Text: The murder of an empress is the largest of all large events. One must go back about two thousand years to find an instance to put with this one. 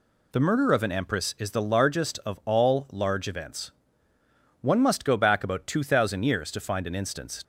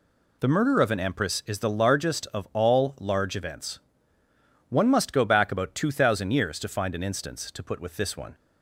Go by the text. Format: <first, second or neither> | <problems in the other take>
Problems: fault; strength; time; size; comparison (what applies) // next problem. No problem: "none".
second | stops before "to put with this one"; at 7.4 s